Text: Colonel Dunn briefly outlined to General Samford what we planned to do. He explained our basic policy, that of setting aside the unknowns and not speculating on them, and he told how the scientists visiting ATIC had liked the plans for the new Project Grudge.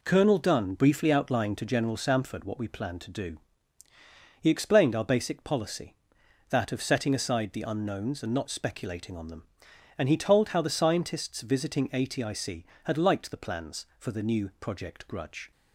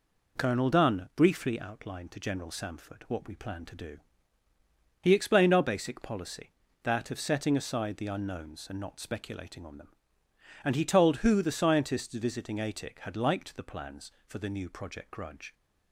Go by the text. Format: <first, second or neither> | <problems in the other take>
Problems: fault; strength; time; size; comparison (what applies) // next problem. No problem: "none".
first | says "who" for "how"; at 11.1 s